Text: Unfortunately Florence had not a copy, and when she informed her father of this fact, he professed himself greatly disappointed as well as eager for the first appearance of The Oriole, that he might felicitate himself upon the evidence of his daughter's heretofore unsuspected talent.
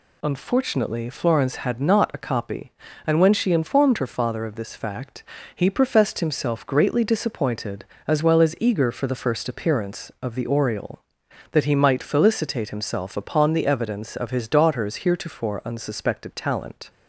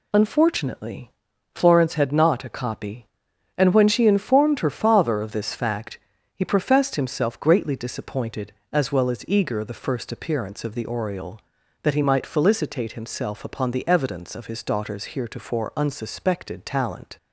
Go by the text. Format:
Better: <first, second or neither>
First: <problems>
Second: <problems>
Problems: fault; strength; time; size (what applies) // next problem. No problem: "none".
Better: first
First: none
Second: pauses between "Unfortunately" and "Florence"; at 1.1 s; 0.42 s long // skips "for"; at 9.6 s